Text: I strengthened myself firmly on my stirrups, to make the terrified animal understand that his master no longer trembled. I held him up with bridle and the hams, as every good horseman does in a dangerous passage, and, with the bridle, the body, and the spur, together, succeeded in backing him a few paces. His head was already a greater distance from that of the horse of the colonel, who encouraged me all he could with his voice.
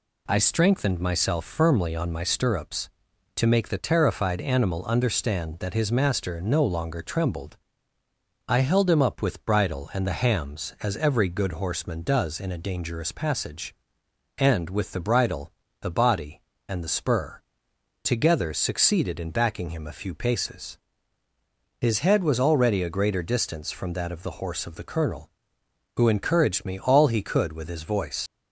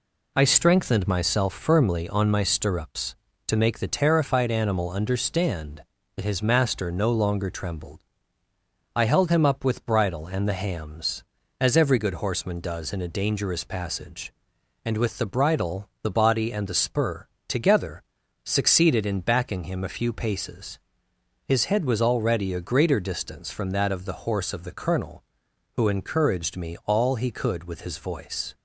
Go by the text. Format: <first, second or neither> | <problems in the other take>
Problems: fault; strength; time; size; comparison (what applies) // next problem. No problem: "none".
second | leaves "voice" unfinished; at 28.2 s; 80 ms